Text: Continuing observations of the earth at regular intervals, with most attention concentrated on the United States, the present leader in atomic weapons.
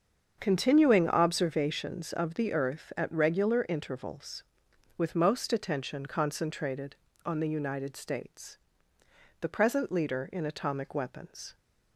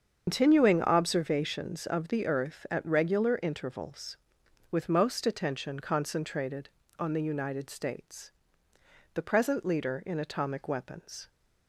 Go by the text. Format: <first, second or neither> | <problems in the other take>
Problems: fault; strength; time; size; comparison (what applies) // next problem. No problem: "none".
first | loses the start of "Continuing"; at 0.2 s; 145 ms // starts louder than the rest; until 1.2 s; 7 dB; also in the first